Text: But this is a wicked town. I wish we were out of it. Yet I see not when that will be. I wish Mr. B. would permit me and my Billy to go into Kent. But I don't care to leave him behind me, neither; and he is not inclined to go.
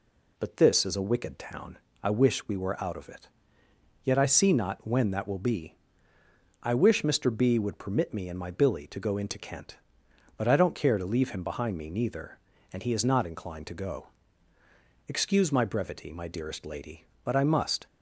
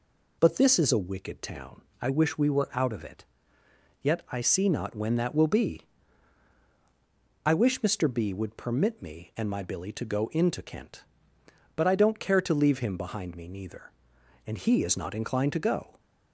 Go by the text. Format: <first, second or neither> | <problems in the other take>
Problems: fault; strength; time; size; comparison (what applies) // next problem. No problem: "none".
second | goes on to say "Excuse my brevity my dearest lady But I must"; strong; from 15.0 s on; 2.7 s long